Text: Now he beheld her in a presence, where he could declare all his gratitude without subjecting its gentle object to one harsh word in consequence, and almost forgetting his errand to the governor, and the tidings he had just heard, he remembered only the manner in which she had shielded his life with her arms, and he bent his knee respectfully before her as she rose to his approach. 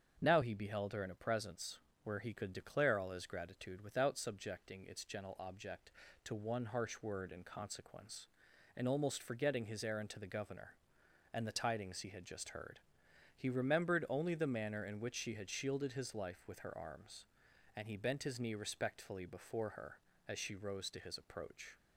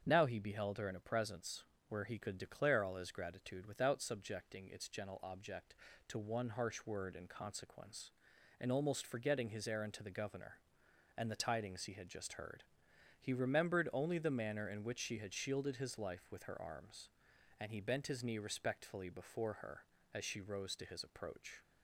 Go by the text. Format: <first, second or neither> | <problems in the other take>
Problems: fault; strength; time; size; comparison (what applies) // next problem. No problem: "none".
neither | starts louder than the rest; strong; the same in both